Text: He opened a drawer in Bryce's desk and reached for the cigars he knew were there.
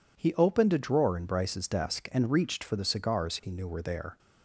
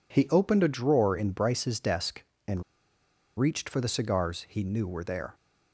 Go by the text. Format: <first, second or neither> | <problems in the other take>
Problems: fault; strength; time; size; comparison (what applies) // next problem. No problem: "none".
first | pauses between "and" and "reached"; noticeable; at 2.6 s; 0.76 s long